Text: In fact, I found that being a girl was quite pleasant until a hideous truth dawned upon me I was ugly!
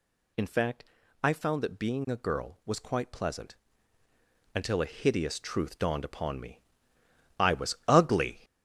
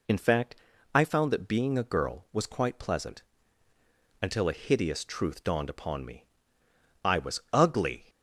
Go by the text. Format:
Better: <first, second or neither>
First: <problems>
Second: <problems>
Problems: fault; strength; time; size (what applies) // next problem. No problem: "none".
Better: second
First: gets louder; throughout; 7 dB // pauses between "pleasant" and "until"; noticeable; at 3.5 s; 0.98 s long // pauses between "me" and "I"; noticeable; at 6.5 s; 0.80 s long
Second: pauses between "pleasant" and "until"; noticeable; at 3.2 s; 0.98 s long // pauses between "me" and "I"; noticeable; at 6.2 s; 0.80 s long